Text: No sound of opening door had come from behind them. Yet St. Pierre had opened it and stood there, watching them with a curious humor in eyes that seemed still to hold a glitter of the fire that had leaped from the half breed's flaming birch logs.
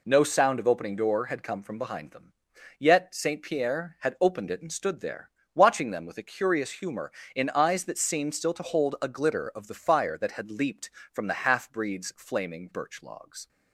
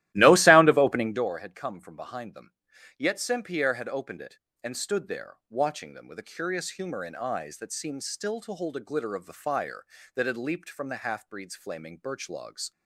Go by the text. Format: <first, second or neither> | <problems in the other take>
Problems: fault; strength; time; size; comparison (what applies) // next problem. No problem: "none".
first | starts louder than the rest; strong; until 1.3 s; 15 dB